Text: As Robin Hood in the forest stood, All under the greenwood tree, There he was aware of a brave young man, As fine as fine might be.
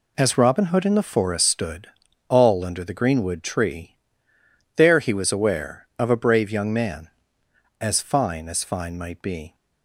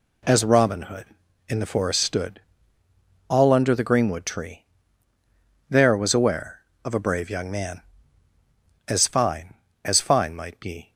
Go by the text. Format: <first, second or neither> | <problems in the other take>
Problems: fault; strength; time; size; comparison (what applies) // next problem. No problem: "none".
first | skips "he"; at 5.9 s